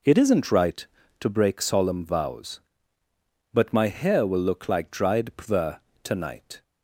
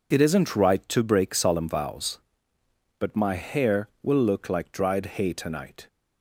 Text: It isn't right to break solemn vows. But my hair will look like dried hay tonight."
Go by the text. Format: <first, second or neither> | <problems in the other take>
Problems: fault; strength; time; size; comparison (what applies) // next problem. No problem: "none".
second | says "pver" for "hay"; at 5.3 s